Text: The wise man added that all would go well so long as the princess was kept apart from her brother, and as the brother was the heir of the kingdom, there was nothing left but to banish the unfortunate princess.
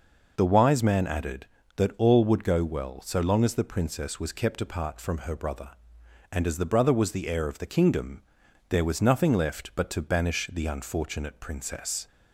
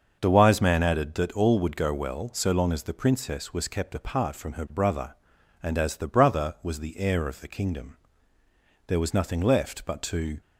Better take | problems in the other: first | starts louder than the rest; until 1.2 s; 6.5 dB // stops before "banish the unfortunate princess"; at 10.4 s

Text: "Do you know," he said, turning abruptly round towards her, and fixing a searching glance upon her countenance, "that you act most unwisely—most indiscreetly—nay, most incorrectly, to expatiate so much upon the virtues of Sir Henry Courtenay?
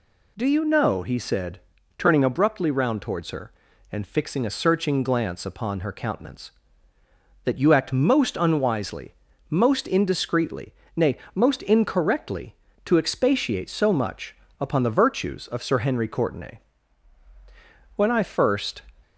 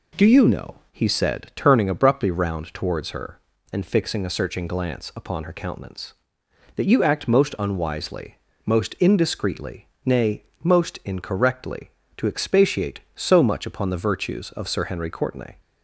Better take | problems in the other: second | pauses between "much" and "upon"; slight; at 14.3 s; 0.24 s long // goes on to say "When I first"; noticeable; from 17.9 s on; 0.88 s long

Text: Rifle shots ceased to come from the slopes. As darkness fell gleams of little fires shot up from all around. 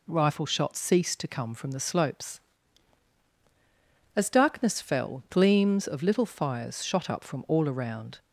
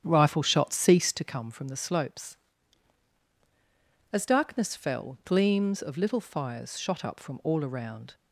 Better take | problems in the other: first | starts louder than the rest; strong; until 1.4 s; 9 dB

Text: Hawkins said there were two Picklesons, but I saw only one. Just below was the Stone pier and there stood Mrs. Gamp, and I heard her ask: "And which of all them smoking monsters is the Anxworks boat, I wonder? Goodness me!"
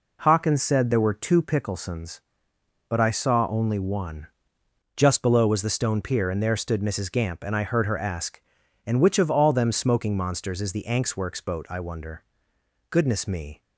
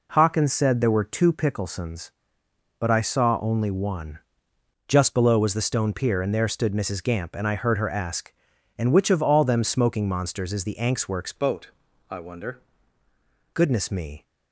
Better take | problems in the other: first | changes voice from "boat" to "wonder"; from 11.3 to 12.5 s; 1.2 s long

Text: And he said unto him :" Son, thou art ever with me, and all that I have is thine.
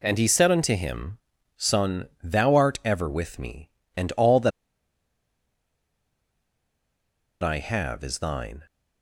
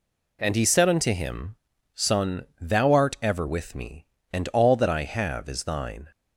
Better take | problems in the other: second | pauses between "that" and "I"; strong; at 4.5 s; 2.9 s long

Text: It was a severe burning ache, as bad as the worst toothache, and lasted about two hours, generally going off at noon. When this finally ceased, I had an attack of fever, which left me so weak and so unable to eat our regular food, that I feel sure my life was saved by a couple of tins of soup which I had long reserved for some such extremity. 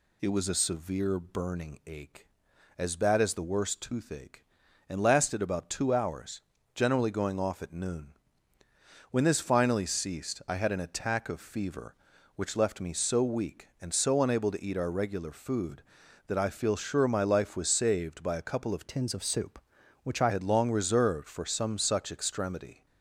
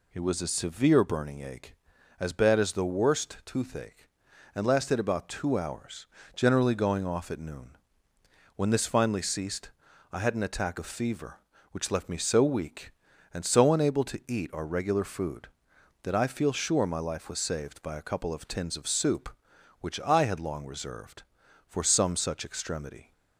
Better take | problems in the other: second | changes voice from "tins" to "I"; from 18.8 to 20.3 s; 1.5 s long

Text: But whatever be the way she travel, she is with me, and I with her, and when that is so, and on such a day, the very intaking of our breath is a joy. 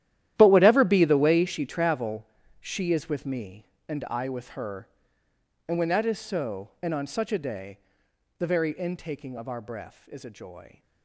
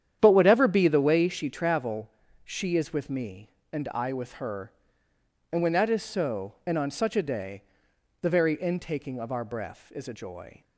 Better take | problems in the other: second | gets quieter; strong; throughout; 16 dB // starts louder than the rest; strong; until 1.3 s; 12.5 dB; strong in the second

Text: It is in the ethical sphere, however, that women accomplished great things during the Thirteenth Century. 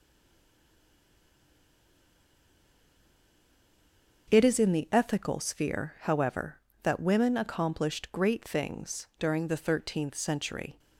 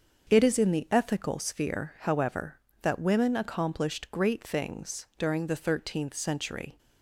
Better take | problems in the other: second | stays silent before the first word; strong; until 4.2 s; 4.2 s long // starts louder than the rest; until 5.3 s; 7 dB; also in the second

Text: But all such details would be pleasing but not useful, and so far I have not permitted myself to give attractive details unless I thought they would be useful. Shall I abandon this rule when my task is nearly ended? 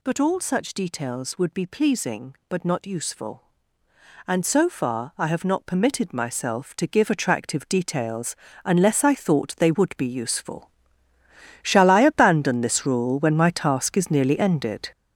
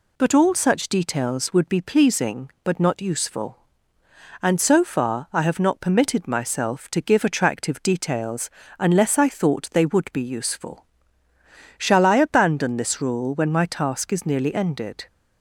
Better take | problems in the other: second | gets louder; strong; throughout; 7.5 dB // pauses between "details" and "unless"; slight; at 8.3 s; 0.28 s long; slight in the second

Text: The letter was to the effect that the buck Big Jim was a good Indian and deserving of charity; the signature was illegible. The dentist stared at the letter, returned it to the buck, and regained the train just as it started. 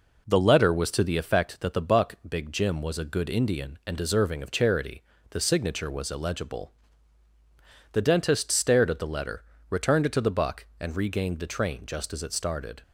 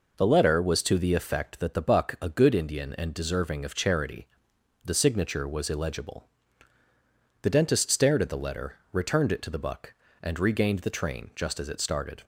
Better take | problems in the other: first | skips "Big Jim was"; at 2.1 s

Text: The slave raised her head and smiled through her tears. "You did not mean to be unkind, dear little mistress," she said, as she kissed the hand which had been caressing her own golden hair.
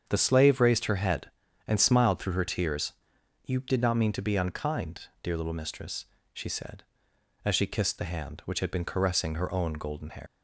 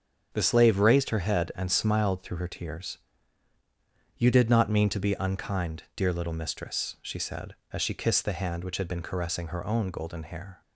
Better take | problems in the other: second | starts louder than the rest; strong; until 1.0 s; 7.5 dB; strong in the second // leaves "hair" unfinished; at 10.2 s; 120 ms

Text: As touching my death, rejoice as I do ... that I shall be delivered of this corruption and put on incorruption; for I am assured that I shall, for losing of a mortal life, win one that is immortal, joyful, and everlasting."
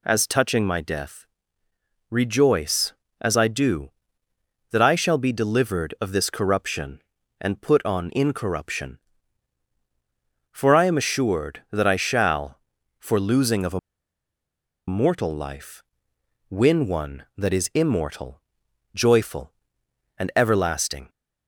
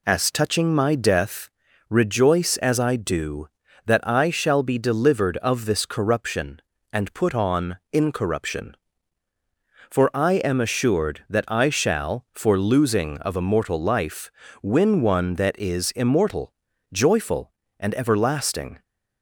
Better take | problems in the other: second | pauses between "a" and "mortal"; at 13.7 s; 1.0 s long

